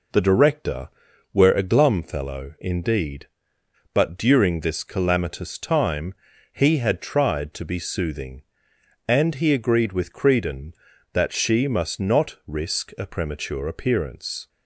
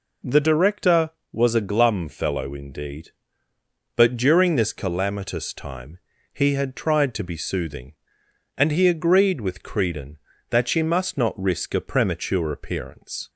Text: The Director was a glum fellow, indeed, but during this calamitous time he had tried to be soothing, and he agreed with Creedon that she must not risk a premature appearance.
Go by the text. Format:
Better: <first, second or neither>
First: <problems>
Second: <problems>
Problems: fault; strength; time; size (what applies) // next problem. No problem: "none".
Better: second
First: says "were" for "was"; at 1.3 s // pauses between "time" and "he"; at 6.1 s; 0.38 s long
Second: pauses between "time" and "he"; slight; at 5.9 s; 0.34 s long